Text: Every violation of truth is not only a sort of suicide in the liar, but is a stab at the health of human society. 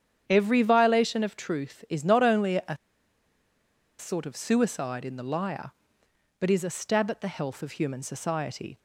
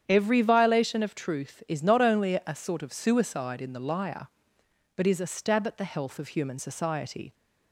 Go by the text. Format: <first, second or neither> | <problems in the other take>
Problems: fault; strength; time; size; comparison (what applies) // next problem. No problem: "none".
second | starts louder than the rest; strong; until 1.2 s; 9 dB; strong in the second // pauses between "a" and "sort"; at 2.7 s; 1.2 s long